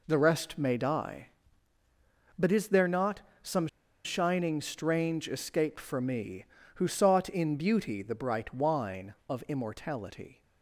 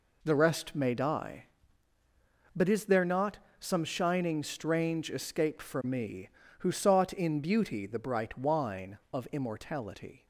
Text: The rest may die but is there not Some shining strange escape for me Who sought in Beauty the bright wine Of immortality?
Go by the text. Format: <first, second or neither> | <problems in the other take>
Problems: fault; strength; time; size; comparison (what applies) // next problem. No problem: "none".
second | pauses between "not" and "Some"; slight; at 3.2 s; 0.18 s long; slight in the second // pauses between "Some" and "shining"; at 3.6 s; 0.38 s long